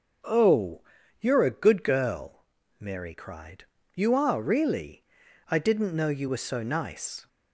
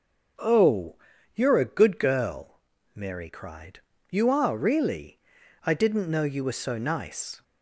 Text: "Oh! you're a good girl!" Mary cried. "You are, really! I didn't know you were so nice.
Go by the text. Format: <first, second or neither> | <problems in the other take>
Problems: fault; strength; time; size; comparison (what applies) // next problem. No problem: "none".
neither | starts louder than the rest; the same in both